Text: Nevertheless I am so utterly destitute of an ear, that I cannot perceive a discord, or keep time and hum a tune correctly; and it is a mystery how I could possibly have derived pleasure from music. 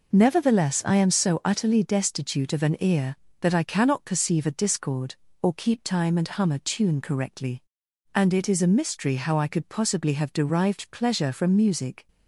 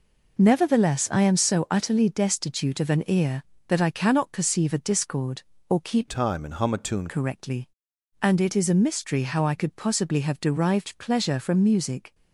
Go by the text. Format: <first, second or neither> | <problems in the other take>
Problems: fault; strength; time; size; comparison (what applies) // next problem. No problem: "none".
first | changes voice from "time" to "tune"; from 6.0 to 7.0 s; 1.0 s long